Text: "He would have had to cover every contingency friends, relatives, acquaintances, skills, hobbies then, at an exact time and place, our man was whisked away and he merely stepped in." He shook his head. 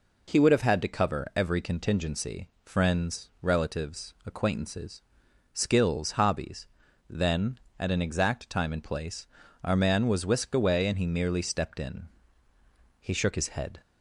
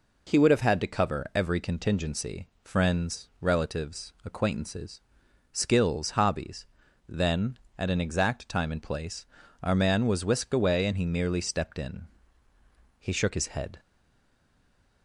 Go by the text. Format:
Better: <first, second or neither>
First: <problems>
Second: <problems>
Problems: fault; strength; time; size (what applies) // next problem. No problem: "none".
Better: first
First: pauses between "hobbies" and "then"; at 6.6 s; 0.42 s long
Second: pauses between "hobbies" and "then"; at 6.6 s; 0.42 s long // stays silent after the last word; noticeable; from 13.7 s on; 1.3 s long